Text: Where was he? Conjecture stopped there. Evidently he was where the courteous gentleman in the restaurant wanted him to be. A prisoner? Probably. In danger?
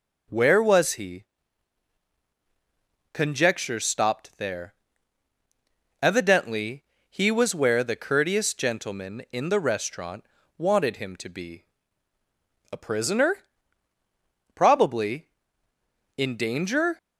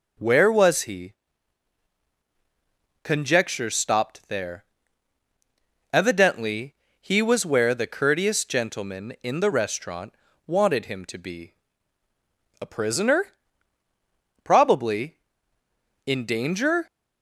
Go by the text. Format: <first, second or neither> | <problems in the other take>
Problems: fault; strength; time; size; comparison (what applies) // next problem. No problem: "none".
neither | pauses between "Evidently" and "he"; slight; the same in both // pauses between "restaurant" and "wanted"; slight; the same in both